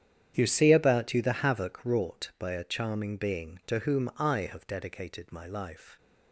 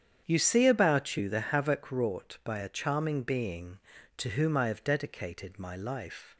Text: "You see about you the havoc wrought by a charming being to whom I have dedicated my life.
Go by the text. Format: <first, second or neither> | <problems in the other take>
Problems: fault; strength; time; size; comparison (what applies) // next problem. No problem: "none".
second | gets quieter; strong; throughout; 15.5 dB // starts louder than the rest; strong; until 1.3 s; 9.5 dB; strong in the second